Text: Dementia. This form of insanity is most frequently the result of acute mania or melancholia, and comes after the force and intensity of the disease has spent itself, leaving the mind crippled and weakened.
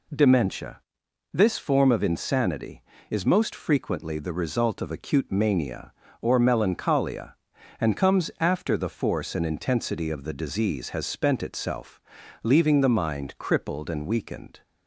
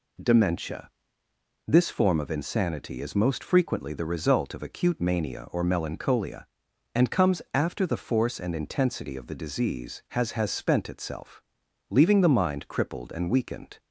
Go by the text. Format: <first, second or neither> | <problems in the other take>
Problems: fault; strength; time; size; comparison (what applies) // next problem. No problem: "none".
first | says "has" twice; at 10.3 s